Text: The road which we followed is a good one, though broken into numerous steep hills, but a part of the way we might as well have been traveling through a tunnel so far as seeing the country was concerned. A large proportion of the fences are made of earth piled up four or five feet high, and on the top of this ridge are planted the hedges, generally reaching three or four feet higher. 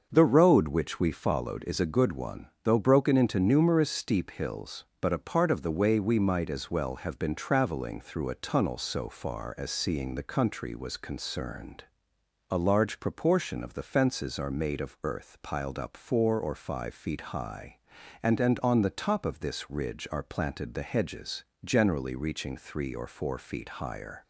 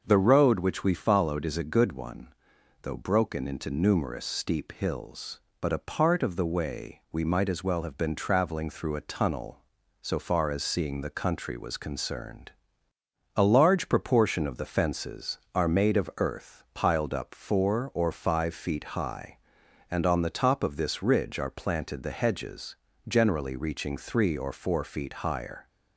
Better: second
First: starts louder than the rest; until 1.1 s; 6.5 dB // says "and" twice; at 18.3 s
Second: starts louder than the rest; until 1.0 s; 6 dB

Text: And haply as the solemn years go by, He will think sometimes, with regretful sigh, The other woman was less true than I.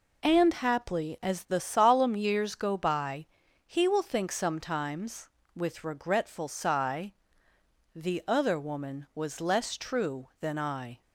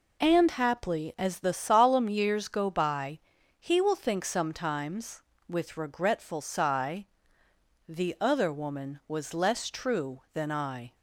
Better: neither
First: none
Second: none

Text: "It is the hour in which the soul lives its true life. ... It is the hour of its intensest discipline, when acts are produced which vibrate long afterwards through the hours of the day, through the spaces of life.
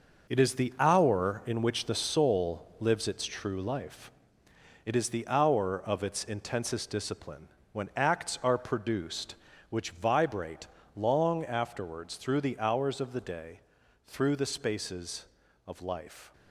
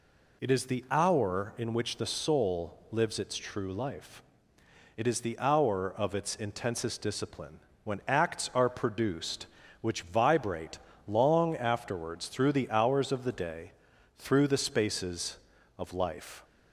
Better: second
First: gets quieter; strong; throughout; 7.5 dB // pauses between "vibrate" and "long"; slight; at 10.6 s; 0.30 s long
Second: pauses between "vibrate" and "long"; slight; at 10.7 s; 0.30 s long

